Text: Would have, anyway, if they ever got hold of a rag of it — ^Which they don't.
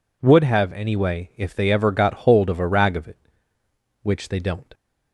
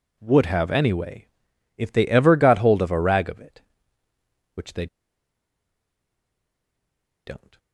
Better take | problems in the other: first | pauses between "they" and "don't"; strong; at 4.8 s; 2.4 s long

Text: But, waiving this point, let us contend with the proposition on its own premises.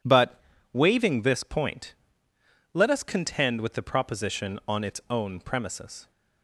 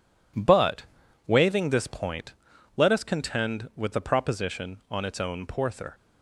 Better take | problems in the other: first | says "porther" for "premises"; at 5.4 s

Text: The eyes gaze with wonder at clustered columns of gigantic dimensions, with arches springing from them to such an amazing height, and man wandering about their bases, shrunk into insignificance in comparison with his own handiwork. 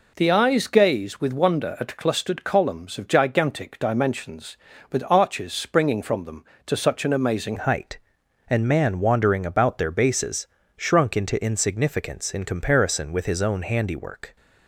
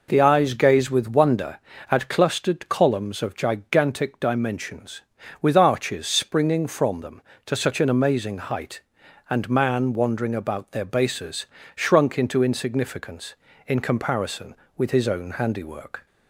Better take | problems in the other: second | changes voice at "height"; from 7.5 s on; 6.8 s long

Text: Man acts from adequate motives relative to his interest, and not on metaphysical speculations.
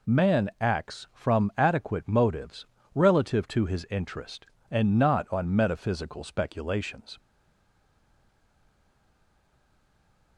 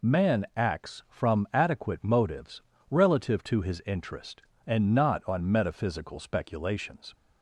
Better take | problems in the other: second | pauses between "motives" and "relative"; slight; at 2.6 s; 0.30 s long; slight in the second // stays silent after the last word; strong; from 7.1 s on; 3.2 s long

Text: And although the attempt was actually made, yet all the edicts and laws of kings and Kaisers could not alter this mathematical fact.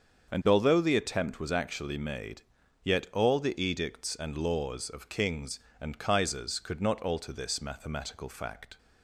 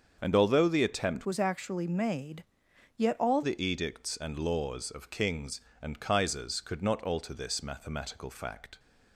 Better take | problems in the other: first | starts louder than the rest; until 1.2 s; 7 dB; also in the first // changes voice from "was" to "all"; from 1.2 to 3.4 s; 2.2 s long

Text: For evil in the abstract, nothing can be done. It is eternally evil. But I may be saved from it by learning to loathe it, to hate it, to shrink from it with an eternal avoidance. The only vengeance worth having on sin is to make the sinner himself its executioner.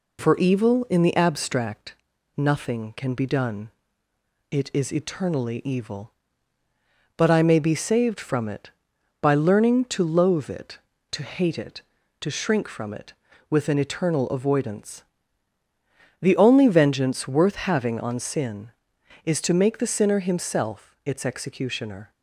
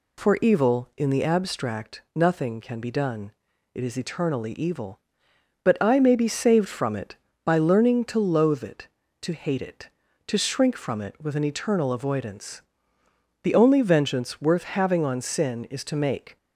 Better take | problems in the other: first | stops before "the sinner himself its executioner"; at 16.3 s

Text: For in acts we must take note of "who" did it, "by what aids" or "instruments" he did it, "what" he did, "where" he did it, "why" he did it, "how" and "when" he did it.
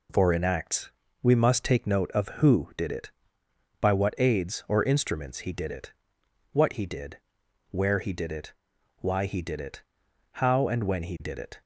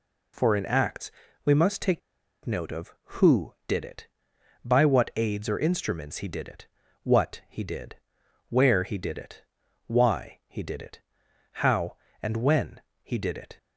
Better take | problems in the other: first | pauses between "acts" and "we"; slight; at 1.1 s; 0.32 s long; slight in the first // pauses between "take" and "note"; at 2.0 s; 0.45 s long // pauses between "when" and "he"; slight; at 12.7 s; 0.22 s long

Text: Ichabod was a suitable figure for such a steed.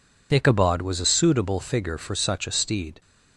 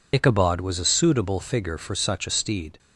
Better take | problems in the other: first | loses the start of "Ichabod"; at 0.1 s; 45 ms

